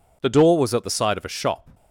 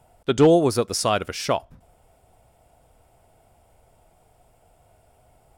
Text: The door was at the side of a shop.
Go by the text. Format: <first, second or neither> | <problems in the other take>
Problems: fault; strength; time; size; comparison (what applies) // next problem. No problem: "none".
first | stays silent after the last word; strong; from 1.7 s on; 3.8 s long